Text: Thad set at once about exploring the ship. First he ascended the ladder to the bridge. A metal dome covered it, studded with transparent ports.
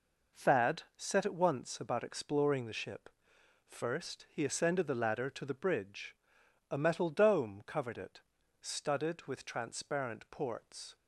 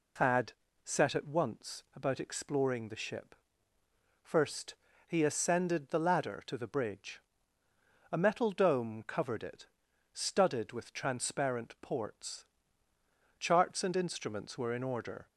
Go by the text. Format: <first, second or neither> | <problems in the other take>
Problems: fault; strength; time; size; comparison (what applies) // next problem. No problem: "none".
first | pauses between "Thad" and "set"; slight; at 0.5 s; 0.30 s long; slight in the first // pauses between "First" and "he"; slight; at 4.7 s; 0.34 s long // goes on to say "Charts and instruments were in order"; strong; from 13.3 s on; 1.8 s long